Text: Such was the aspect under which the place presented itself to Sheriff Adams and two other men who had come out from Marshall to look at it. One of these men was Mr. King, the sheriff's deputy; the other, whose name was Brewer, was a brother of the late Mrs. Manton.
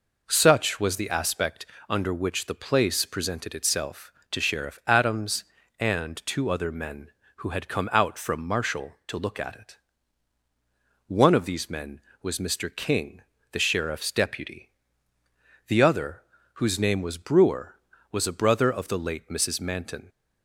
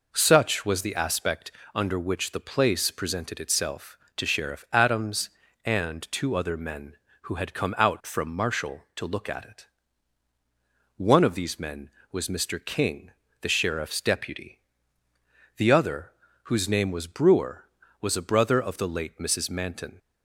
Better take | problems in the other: neither | pauses between "aspect" and "under"; slight; the same in both

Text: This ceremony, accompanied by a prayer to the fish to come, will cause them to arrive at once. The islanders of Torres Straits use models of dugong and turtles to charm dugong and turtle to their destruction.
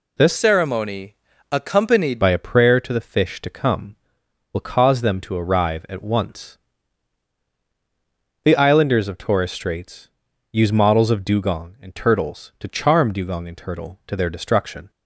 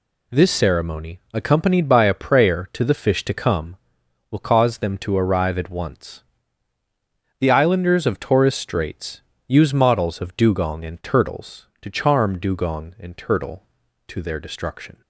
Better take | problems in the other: second | changes voice from "ceremony" to "accompanied"; from 0.3 to 2.2 s; 1.9 s long // pauses between "Straits" and "use"; at 10.0 s; 0.42 s long; slight in the second

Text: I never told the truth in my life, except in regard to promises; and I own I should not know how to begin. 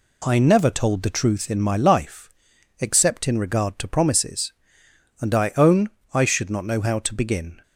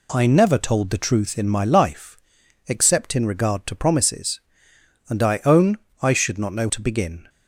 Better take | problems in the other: first | pauses between "own" and "I"; slight; at 5.7 s; 0.24 s long; slight in the first // skips "how"; at 6.6 s

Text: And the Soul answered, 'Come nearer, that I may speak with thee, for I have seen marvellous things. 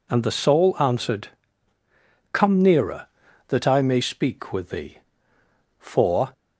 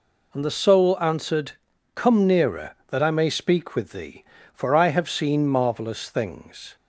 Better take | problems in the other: second | stops before "I have seen marvellous things"; at 6.3 s

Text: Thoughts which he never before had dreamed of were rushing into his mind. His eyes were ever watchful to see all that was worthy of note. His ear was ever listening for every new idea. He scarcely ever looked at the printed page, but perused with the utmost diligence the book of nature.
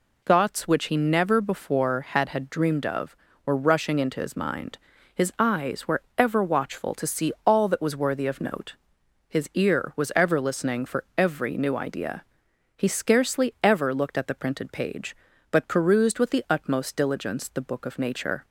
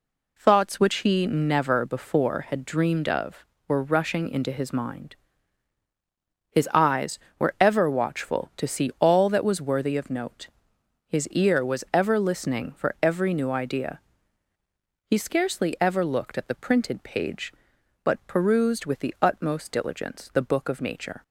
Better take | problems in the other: second | says "had" twice; at 2.2 s

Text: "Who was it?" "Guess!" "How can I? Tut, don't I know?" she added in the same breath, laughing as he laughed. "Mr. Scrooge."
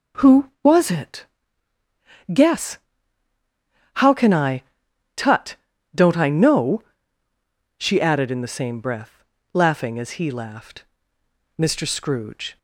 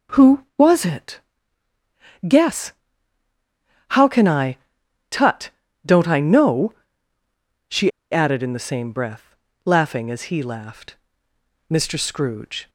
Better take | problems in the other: first | pauses between "she" and "added"; slight; at 7.9 s; 0.22 s long

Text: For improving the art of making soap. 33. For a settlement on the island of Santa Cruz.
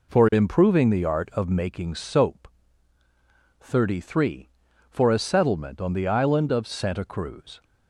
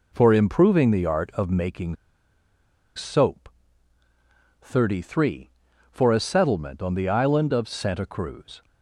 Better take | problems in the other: first | pauses between "making" and "soap"; at 1.9 s; 1.0 s long

